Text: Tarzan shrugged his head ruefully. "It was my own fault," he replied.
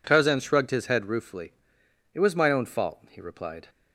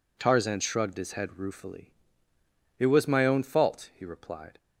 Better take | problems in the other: neither | none

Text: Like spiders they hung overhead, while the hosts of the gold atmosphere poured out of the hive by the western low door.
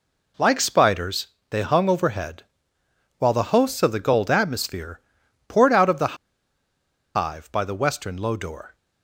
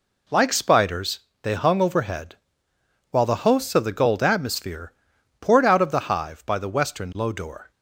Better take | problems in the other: second | pauses between "spiders" and "they"; slight; at 1.2 s; 0.22 s long; slight in the second // pauses between "atmosphere" and "poured"; noticeable; at 4.9 s; 0.48 s long; noticeable in the second // pauses between "the" and "hive"; at 6.1 s; 0.99 s long

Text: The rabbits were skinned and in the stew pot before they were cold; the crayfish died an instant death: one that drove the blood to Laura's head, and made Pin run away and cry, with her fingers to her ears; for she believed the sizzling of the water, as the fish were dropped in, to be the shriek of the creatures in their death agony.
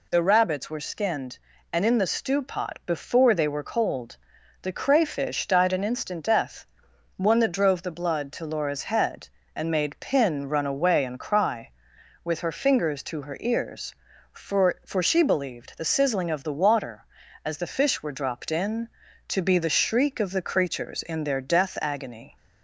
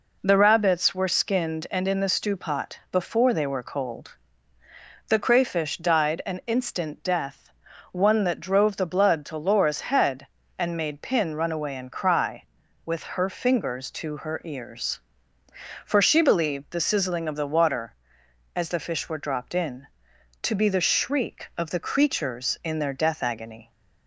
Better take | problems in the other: second | says "for" twice; at 14.8 s

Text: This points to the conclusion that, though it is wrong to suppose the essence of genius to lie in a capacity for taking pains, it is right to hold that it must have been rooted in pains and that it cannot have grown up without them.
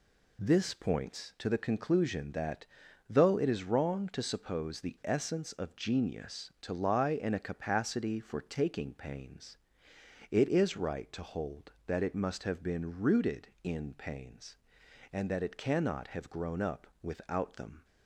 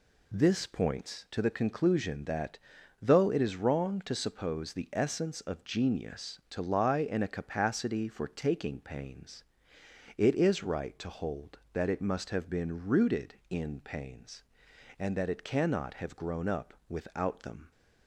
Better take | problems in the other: neither | none

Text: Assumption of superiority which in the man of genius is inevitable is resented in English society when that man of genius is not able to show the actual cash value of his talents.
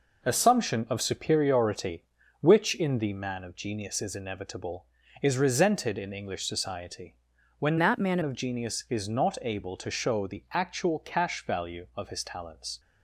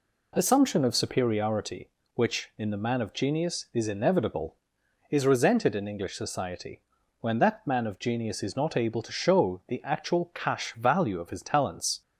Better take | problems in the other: second | pauses between "society" and "when"; at 7.1 s; 0.42 s long; also in the second // changes voice from "that" to "man"; from 7.7 to 8.1 s; 0.4 s long

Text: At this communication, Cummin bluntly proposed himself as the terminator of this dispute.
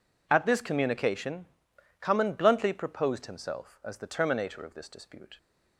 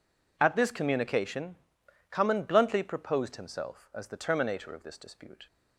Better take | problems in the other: neither | none

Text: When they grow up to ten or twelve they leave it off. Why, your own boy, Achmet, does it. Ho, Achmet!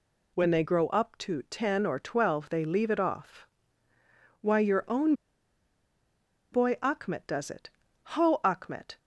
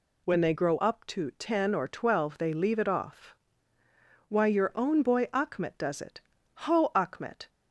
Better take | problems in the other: second | pauses between "own" and "boy"; strong; at 5.1 s; 1.3 s long

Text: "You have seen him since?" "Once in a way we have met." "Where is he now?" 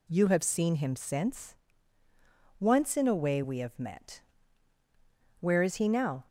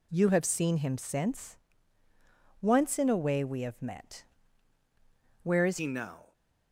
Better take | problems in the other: first | changes voice at "he"; from 5.7 s on; 0.6 s long

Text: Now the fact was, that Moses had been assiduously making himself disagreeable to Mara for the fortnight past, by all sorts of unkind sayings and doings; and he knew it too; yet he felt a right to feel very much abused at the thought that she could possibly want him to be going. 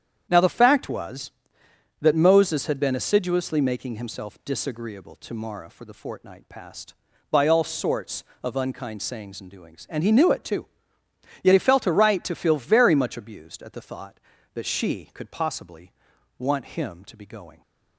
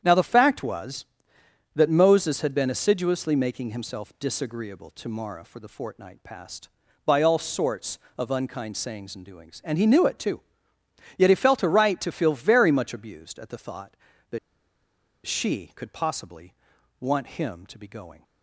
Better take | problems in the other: first | starts louder than the rest; strong; until 1.0 s; 9 dB; strong in the first // pauses between "that" and "she"; noticeable; at 14.3 s; 0.88 s long // pauses between "possibly" and "want"; at 16.5 s; 0.44 s long; also in the first

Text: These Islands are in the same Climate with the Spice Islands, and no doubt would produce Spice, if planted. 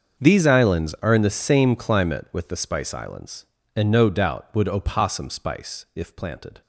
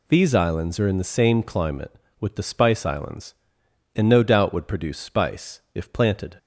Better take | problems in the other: second | starts louder than the rest; until 1.2 s; 6.5 dB // says "opossum" for "produce"; at 4.6 s

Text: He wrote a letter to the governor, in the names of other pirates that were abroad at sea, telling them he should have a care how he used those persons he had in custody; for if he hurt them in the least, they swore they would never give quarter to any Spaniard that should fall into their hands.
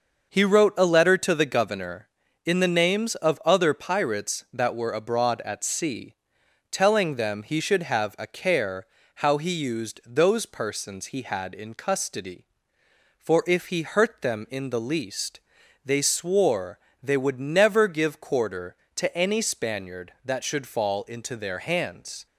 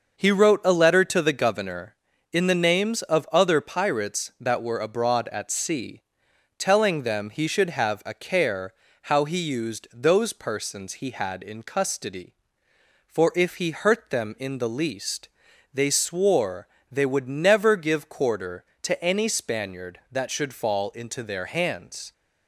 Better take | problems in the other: neither | starts louder than the rest; noticeable; the same in both // pauses between "care" and "how"; slight; the same in both // pauses between "swore" and "they"; slight; the same in both

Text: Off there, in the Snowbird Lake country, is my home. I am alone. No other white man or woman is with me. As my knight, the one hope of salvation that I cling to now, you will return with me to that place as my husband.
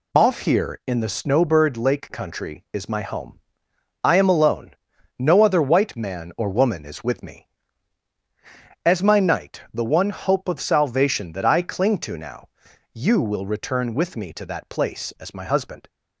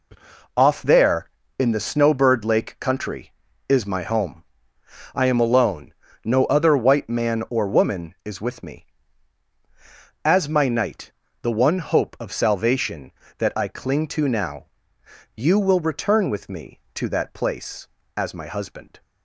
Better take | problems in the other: second | says "here" for "there"; at 0.4 s

